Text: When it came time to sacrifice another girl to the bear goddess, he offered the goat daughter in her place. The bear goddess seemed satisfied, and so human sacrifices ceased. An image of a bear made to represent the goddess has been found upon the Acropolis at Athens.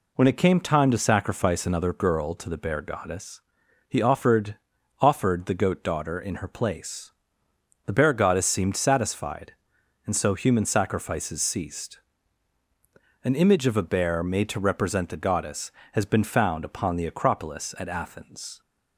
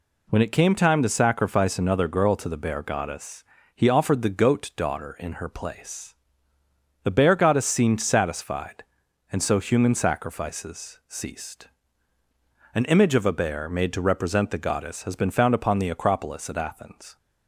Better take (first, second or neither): second